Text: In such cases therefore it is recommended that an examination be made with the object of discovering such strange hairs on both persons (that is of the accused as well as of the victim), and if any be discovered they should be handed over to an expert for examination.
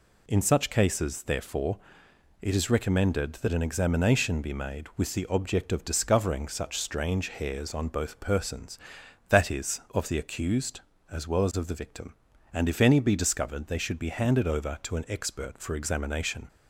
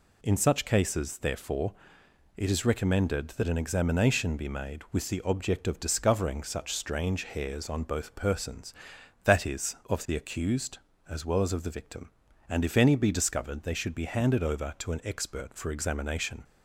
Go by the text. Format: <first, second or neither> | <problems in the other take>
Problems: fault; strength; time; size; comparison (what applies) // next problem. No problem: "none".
neither | pauses between "therefore" and "it"; noticeable; the same in both